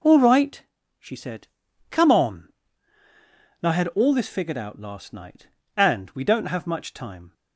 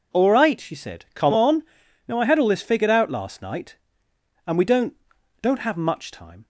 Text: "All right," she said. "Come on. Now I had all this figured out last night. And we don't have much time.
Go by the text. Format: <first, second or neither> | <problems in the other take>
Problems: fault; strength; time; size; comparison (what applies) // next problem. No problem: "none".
first | says "don't" twice; at 5.4 s